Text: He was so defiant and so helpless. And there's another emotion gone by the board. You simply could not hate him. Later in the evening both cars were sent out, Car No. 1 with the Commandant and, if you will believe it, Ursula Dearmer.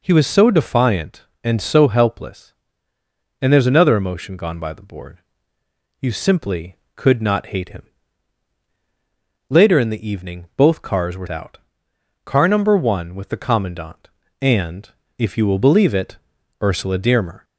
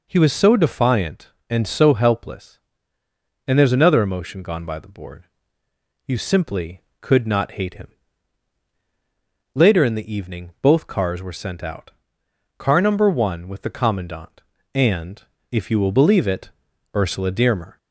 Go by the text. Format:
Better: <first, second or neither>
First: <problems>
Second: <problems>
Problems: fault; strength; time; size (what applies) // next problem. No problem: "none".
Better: second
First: skips "sent"; at 11.2 s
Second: none